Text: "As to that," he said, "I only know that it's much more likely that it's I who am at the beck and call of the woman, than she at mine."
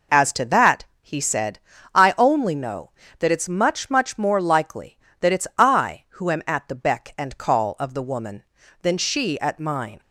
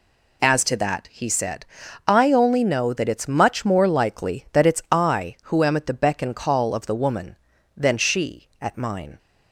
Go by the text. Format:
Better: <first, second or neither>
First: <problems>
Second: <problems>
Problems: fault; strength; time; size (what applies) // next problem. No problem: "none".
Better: second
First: says "much" twice; at 3.9 s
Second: none